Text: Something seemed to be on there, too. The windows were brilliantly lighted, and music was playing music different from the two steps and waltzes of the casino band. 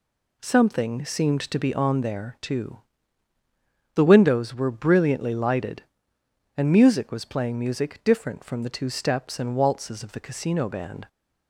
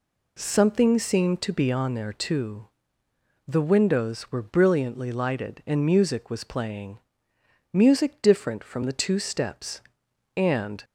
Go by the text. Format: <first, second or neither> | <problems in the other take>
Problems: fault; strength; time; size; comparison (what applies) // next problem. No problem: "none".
first | pauses between "playing" and "music"; noticeable; at 6.9 s; 0.74 s long // stops before "waltzes of the casino band"; at 10.8 s